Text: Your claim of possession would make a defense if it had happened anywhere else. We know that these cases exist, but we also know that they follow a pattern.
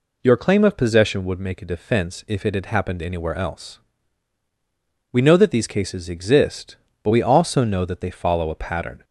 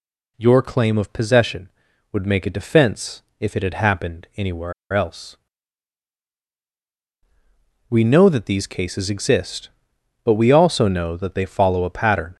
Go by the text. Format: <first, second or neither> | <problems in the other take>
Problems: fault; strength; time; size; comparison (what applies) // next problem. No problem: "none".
first | pauses between "defense" and "if"; slight; at 3.2 s; 0.16 s long // pauses between "anywhere" and "else"; slight; at 4.7 s; 0.20 s long